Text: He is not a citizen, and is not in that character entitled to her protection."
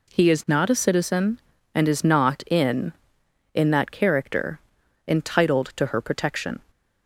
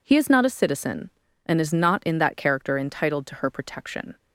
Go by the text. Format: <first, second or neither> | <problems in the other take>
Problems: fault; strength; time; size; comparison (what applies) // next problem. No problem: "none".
second | says "in" twice; at 3.5 s // pauses between "character" and "entitled"; noticeable; at 4.5 s; 0.48 s long